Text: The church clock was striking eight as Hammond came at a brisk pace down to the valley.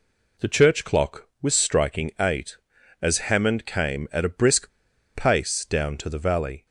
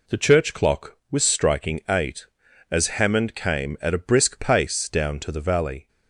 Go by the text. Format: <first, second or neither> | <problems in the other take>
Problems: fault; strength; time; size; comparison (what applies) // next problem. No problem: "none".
second | pauses between "brisk" and "pace"; at 4.6 s; 0.45 s long